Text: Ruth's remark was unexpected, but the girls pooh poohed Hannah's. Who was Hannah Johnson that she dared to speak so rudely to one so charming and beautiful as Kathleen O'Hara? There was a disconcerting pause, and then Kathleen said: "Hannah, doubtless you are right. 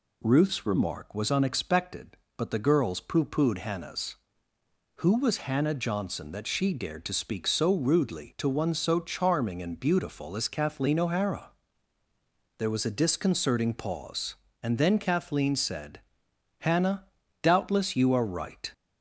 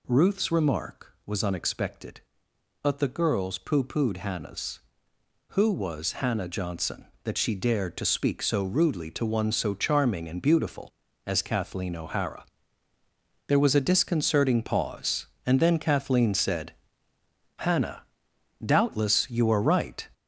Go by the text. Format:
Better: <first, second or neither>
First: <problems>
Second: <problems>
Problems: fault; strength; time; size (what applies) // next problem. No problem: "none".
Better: first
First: none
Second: gets louder; noticeable; throughout; 6 dB